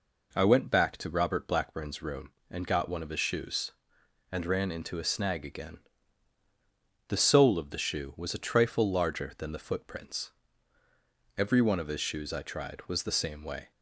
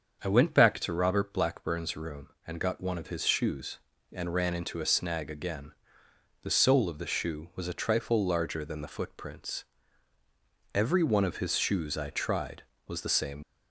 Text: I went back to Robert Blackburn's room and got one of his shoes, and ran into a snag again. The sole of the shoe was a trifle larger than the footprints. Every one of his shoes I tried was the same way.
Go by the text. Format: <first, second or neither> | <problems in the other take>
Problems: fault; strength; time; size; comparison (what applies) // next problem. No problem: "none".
first | starts louder than the rest; until 1.2 s; 7 dB // stops before "way"; at 13.4 s